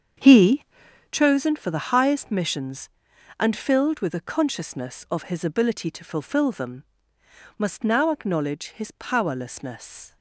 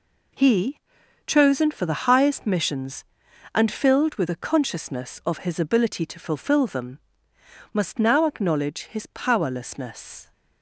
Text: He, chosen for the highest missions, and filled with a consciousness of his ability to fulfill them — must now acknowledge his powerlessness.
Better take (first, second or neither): second